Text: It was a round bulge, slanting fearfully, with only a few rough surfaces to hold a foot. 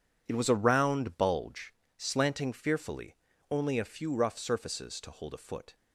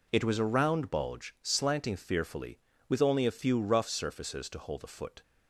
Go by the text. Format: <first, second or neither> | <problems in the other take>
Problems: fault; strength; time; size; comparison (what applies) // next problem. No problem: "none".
second | skips "with"; at 3.3 s